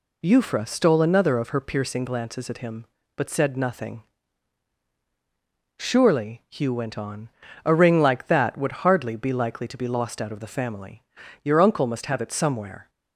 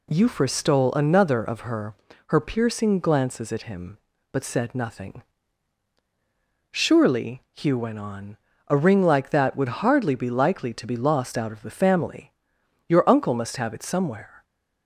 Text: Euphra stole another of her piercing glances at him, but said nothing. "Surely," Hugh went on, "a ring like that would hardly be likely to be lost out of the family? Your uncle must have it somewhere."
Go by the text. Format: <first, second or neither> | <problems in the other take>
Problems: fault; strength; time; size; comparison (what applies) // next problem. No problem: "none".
first | says "her" twice; at 2.2 s